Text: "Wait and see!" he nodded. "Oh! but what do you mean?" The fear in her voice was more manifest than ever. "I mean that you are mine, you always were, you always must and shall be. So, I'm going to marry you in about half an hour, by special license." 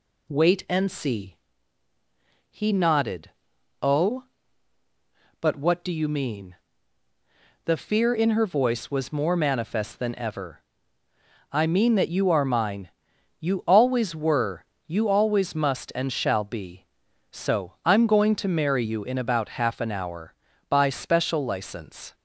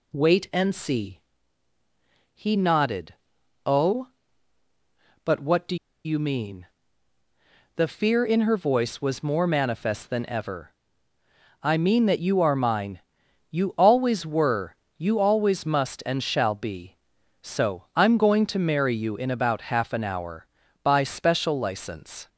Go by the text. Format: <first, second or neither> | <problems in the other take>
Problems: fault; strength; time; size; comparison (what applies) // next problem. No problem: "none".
first | pauses between "do" and "you"; slight; at 5.7 s; 0.29 s long